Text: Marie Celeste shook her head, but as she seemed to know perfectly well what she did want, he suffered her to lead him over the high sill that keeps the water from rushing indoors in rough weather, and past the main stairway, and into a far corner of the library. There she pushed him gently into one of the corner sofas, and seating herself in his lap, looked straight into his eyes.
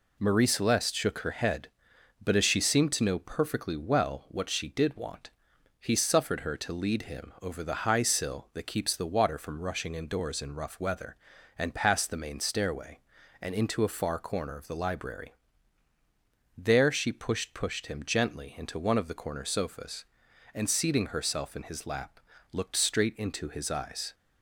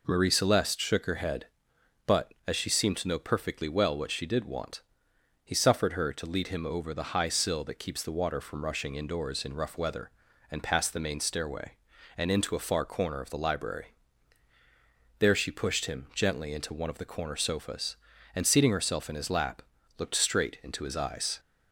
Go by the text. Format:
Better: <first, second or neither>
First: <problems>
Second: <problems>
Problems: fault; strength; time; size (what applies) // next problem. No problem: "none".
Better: second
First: says "pushed" twice; at 17.5 s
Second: none